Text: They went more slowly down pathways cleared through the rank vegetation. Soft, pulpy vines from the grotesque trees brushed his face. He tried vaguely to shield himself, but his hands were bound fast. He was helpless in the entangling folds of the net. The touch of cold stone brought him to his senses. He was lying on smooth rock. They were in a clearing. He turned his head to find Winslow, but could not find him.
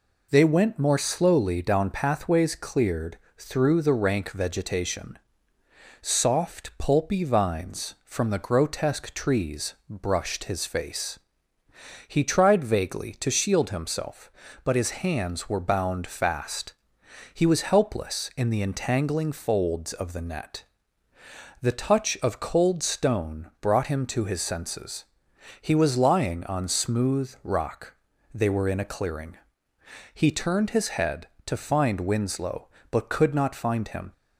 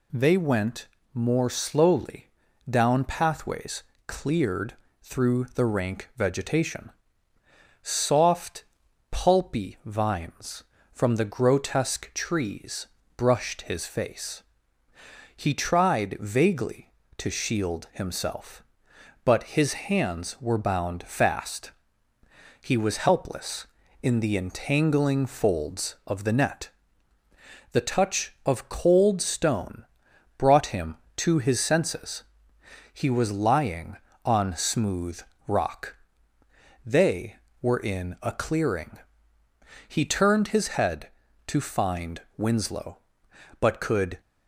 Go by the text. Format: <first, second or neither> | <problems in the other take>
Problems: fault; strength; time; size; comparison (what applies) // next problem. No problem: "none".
first | pauses between "went" and "more"; slight; at 0.8 s; 0.26 s long // pauses between "slowly" and "down"; at 2.2 s; 0.40 s long // pauses between "pathways" and "cleared"; slight; at 3.8 s; 0.24 s long // pauses between "cleared" and "through"; slight; at 4.7 s; 0.28 s long; slight in the first // pauses between "trees" and "brushed"; slight; at 12.8 s; 0.30 s long // pauses between "stone" and "brought"; noticeable; at 29.8 s; 0.52 s long // pauses between "smooth" and "rock"; slight; at 35.1 s; 0.26 s long // stops before "not find him"; at 44.1 s